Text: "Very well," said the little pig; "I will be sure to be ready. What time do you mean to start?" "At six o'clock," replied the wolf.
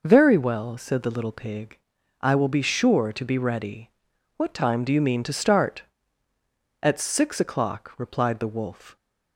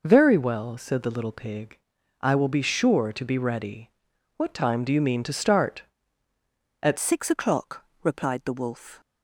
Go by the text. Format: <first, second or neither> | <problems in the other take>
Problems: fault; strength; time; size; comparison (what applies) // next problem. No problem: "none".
first | changes voice at "six"; from 6.9 s on; 2.1 s long